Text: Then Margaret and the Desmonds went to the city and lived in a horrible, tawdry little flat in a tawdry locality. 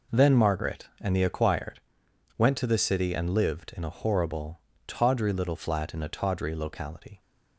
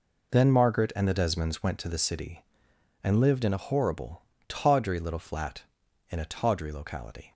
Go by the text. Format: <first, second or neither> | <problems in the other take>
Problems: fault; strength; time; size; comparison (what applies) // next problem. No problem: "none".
second | says "Acquired" for "Desmonds"; at 1.2 s